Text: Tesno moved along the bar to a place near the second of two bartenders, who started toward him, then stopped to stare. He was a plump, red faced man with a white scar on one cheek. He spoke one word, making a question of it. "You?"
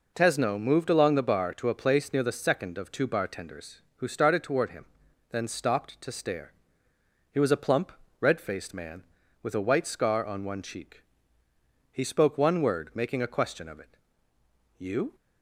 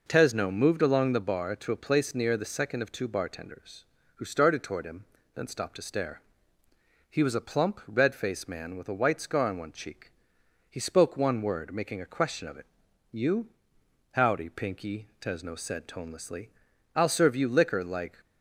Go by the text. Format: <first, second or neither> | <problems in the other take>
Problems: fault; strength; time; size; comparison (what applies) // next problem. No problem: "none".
first | goes on to say "Howdy Pinky Tesno said tonelessly I'll serve you liquor like"; strong; from 14.1 s on; 4.0 s long